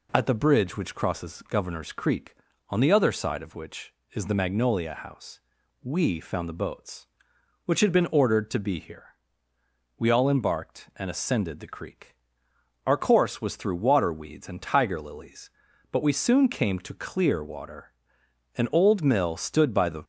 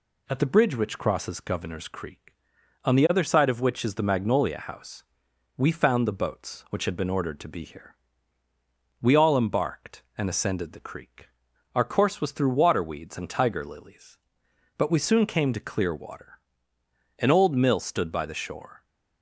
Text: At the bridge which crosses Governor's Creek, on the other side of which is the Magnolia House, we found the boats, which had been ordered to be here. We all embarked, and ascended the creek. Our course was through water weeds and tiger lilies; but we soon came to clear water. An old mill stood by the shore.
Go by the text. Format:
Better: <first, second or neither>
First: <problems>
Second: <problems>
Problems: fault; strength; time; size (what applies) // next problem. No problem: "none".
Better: second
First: stops before "shore"; at 20.0 s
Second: none